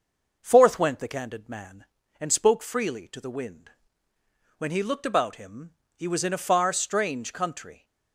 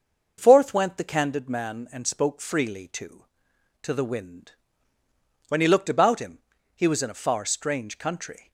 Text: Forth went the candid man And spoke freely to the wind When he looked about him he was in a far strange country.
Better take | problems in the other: first | starts louder than the rest; noticeable; until 1.3 s; 6 dB // says "to" twice; at 3.8 s // pauses between "wind" and "When"; noticeable; at 4.5 s; 0.96 s long; noticeable in the first // pauses between "him" and "he"; at 6.3 s; 0.40 s long; slight in the first

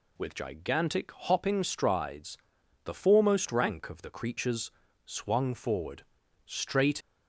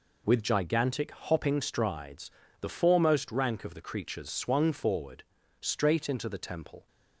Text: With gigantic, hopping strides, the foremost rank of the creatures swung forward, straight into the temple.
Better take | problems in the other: second | pauses between "creatures" and "swung"; slight; at 4.7 s; 0.32 s long // stops before "into the temple"; at 7.0 s

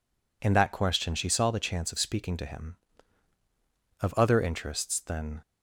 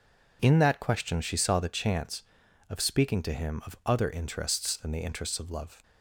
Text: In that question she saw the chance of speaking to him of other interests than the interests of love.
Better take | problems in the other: second | stops before "the interests of love"; at 5.4 s

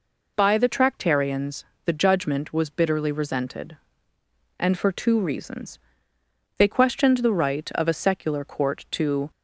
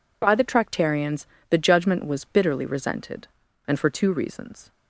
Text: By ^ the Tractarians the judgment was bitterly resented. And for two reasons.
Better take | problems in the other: second | pauses between "Tractarians" and "the"; slight; at 1.6 s; 0.20 s long; slight in the second // goes on to say "They questioned the right of a secular Court to"; strong; from 6.5 s on; 2.7 s long

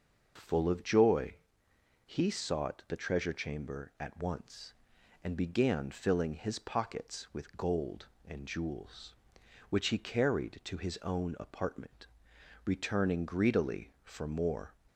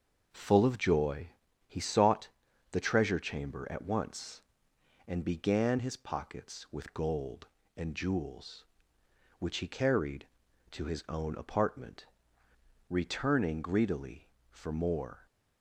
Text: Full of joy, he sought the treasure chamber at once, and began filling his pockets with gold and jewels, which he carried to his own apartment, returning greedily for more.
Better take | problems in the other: first | starts louder than the rest; until 1.7 s; 6.5 dB // pauses between "sought" and "the"; at 2.2 s; 0.42 s long // skips "filling"; at 5.7 s

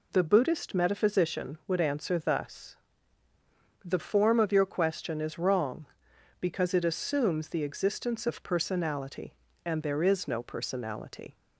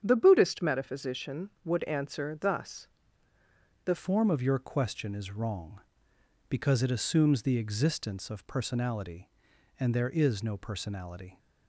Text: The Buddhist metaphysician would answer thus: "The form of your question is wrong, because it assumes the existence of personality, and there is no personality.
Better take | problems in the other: first | starts louder than the rest; strong; until 1.0 s; 8.5 dB // changes voice at "form"; from 3.9 s on; 7.4 s long

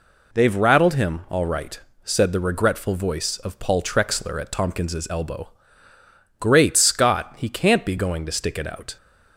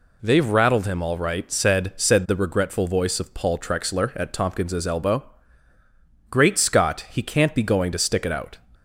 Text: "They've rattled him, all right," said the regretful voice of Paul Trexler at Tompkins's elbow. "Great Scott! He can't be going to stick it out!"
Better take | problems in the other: first | says "said" twice; at 1.9 s

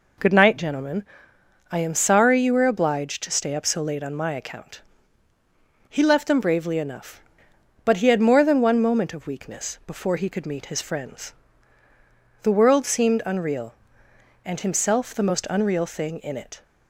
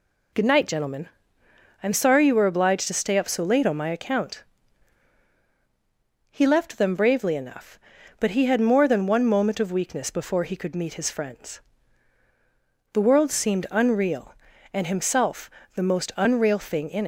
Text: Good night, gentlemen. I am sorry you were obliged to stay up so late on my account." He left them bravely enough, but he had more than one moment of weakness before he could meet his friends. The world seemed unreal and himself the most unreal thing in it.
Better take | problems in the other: first | pauses between "himself" and "the"; slight; at 15.4 s; 0.26 s long // stops before "it"; at 17.0 s

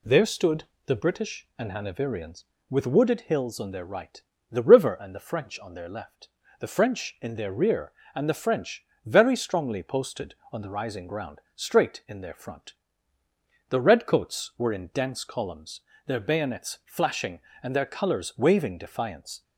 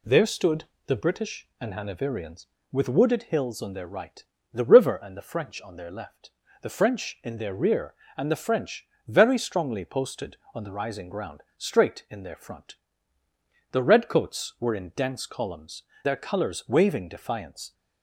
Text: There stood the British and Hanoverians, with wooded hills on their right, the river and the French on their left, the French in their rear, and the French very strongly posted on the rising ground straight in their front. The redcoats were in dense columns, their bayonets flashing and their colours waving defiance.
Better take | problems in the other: first | pauses between "stood" and "the"; slight; at 0.6 s; 0.20 s long; slight in the first // pauses between "French" and "very"; slight; at 8.8 s; 0.20 s long; slight in the first // pauses between "ground" and "straight"; slight; at 11.4 s; 0.16 s long; slight in the first // skips "their bayonets flashing and"; at 15.9 s

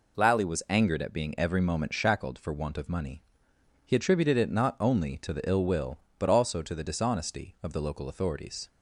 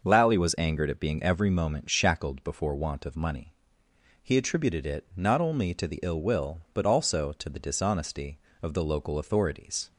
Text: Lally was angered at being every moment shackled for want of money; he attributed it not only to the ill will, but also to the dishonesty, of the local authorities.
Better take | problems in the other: first | starts louder than the rest; noticeable; until 1.0 s; 6 dB // says "before" for "for"; at 2.4 s

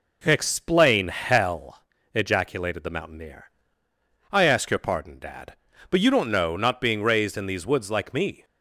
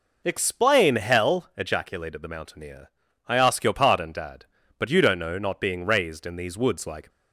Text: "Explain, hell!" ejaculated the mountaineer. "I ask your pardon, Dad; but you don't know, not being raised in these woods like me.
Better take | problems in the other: first | stops before "me"; at 7.1 s

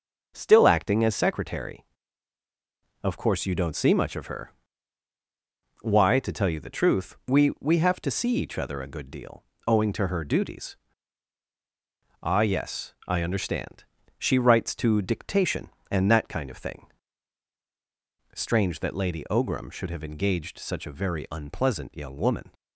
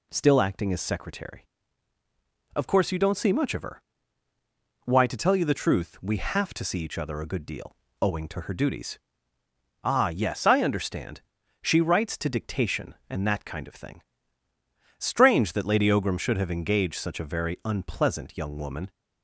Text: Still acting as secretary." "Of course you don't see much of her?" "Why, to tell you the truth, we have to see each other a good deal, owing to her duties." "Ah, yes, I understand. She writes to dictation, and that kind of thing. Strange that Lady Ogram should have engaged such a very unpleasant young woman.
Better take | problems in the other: second | says "we" twice; at 7.5 s

